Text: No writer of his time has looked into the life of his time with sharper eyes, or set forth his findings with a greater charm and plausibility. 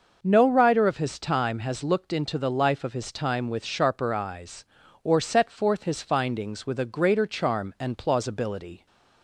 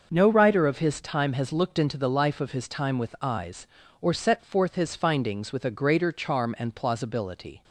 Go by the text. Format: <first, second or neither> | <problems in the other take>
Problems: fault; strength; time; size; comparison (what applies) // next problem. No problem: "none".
first | starts louder than the rest; noticeable; until 1.1 s; 6 dB // skips "sharper"; at 3.1 s